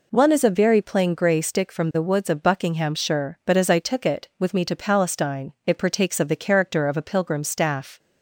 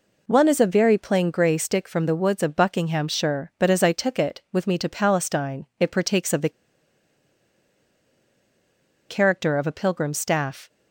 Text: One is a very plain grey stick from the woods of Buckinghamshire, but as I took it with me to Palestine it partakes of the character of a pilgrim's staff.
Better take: first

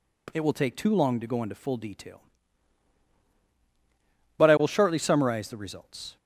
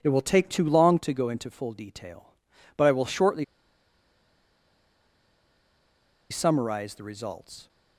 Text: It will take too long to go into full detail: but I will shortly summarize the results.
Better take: first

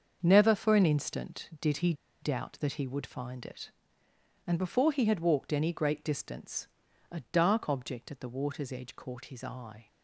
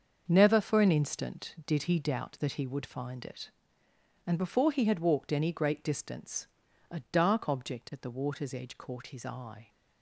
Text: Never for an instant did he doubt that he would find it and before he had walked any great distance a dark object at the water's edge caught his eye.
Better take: second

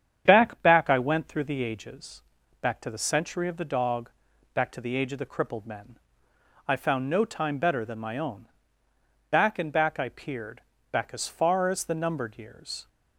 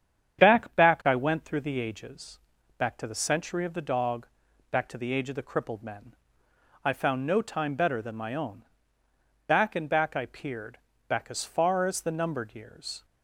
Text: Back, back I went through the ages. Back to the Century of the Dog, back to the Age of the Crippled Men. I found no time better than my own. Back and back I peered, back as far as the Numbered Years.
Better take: neither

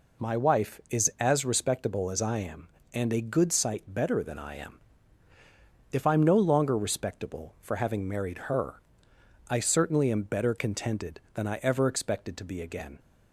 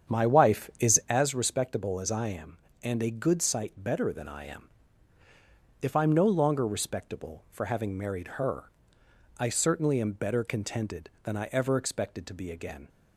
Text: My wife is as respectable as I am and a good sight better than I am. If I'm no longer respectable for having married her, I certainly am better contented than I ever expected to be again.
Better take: first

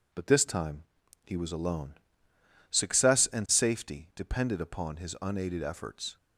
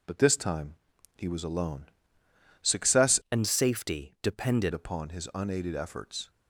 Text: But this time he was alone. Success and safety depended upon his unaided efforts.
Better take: first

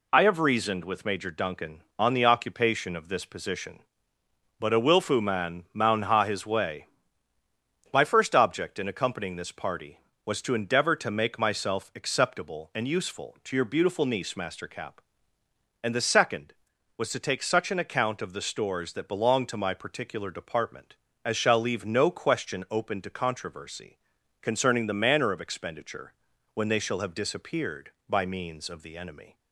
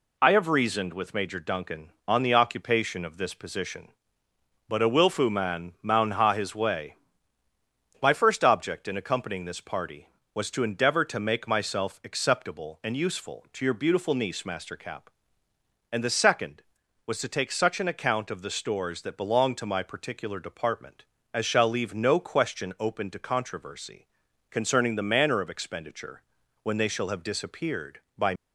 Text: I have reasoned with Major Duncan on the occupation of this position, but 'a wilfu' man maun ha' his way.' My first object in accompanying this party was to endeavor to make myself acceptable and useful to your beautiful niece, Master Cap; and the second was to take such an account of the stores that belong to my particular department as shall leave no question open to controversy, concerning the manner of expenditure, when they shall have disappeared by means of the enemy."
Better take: first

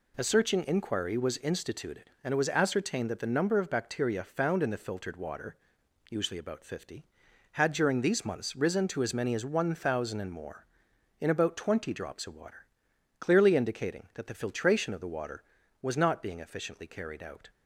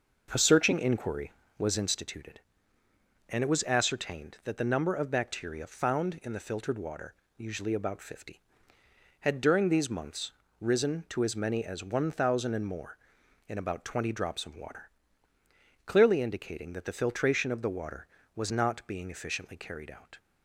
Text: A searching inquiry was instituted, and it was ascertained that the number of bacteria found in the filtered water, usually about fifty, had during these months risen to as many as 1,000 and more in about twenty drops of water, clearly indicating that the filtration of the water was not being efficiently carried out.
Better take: first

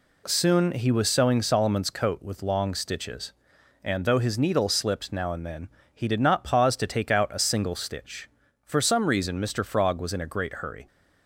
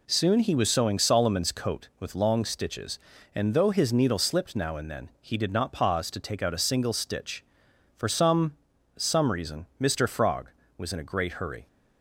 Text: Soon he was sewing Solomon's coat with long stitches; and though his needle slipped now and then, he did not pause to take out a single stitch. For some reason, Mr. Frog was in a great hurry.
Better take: first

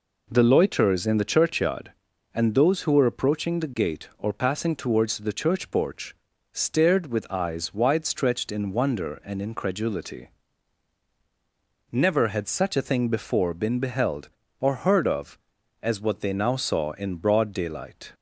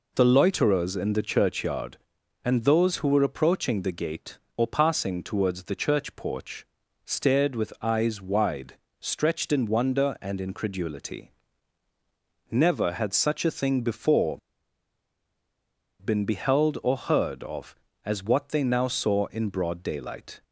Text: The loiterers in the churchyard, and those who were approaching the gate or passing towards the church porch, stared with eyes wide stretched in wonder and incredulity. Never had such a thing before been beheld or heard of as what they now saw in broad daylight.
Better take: first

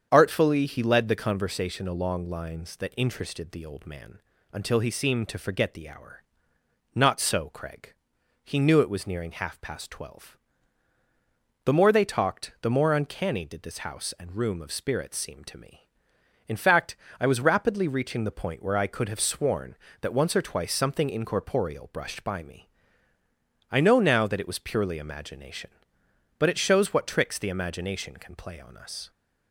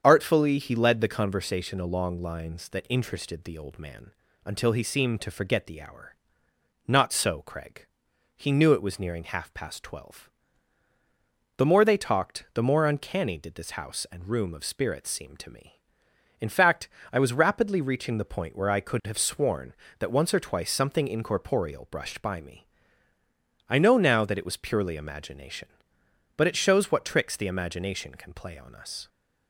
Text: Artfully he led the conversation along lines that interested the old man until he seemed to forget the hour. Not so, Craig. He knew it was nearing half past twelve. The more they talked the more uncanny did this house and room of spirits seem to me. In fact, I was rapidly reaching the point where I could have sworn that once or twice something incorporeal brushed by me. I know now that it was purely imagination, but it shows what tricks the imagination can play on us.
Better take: neither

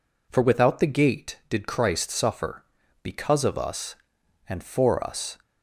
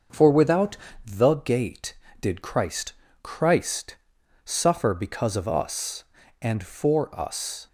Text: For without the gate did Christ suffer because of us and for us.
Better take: first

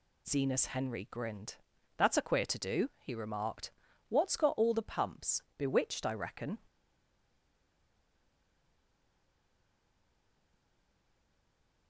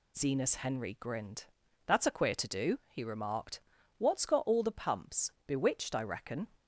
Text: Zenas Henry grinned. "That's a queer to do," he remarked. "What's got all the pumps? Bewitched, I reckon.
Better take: second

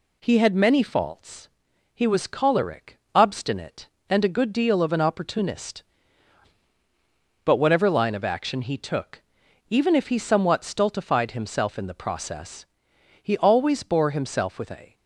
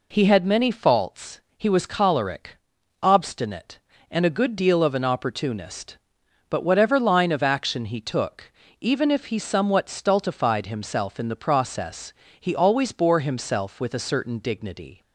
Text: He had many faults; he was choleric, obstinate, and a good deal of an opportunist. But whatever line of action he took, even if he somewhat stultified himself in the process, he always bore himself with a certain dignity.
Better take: second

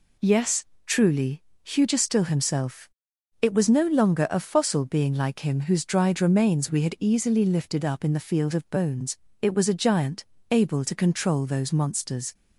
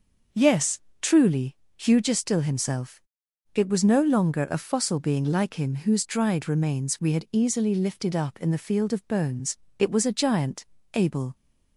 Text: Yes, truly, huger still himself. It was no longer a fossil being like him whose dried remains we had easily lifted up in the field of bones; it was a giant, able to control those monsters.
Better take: first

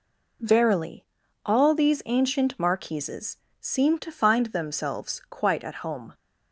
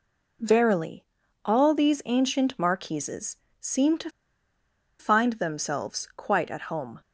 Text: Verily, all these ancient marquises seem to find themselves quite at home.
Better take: first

